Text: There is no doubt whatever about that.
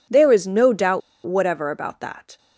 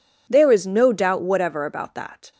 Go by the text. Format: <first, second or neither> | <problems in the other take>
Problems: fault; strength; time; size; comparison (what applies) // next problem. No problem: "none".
second | pauses between "doubt" and "whatever"; slight; at 1.0 s; 0.24 s long